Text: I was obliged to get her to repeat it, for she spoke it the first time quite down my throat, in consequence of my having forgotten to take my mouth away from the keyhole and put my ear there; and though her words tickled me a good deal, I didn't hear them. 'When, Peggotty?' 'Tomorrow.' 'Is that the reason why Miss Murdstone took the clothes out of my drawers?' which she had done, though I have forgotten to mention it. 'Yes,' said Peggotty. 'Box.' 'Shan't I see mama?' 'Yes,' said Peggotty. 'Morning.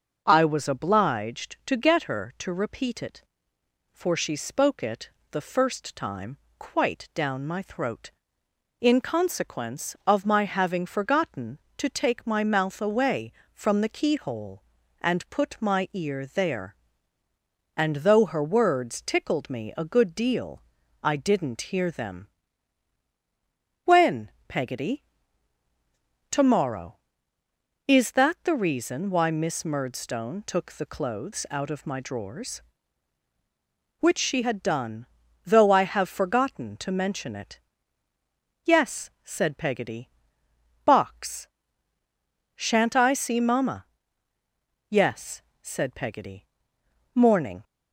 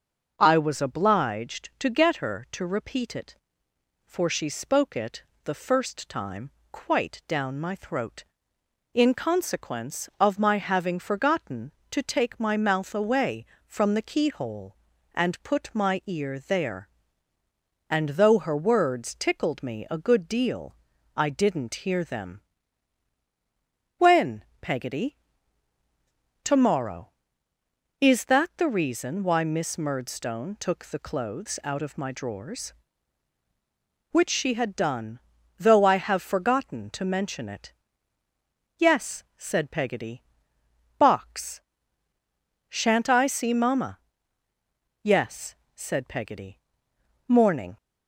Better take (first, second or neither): neither